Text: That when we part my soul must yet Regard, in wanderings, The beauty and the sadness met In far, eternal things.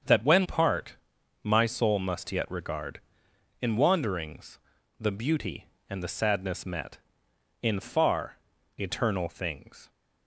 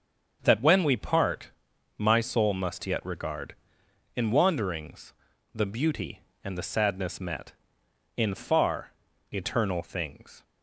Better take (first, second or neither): second